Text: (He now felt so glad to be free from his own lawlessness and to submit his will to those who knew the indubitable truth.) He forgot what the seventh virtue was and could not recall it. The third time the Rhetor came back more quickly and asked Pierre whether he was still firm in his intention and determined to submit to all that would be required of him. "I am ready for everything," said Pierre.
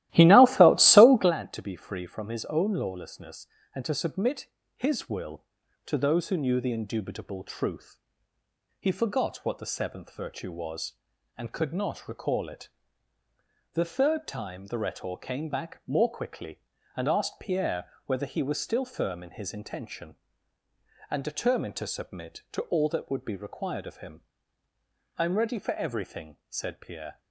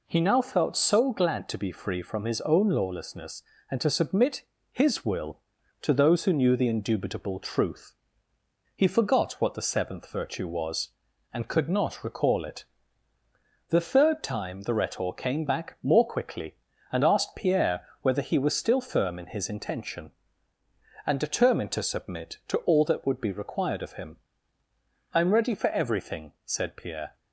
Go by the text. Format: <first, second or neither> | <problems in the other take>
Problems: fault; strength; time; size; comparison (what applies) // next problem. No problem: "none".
second | starts louder than the rest; strong; until 1.4 s; 15.5 dB // pauses between "submit" and "his"; slight; at 4.4 s; 0.28 s long; slight in the second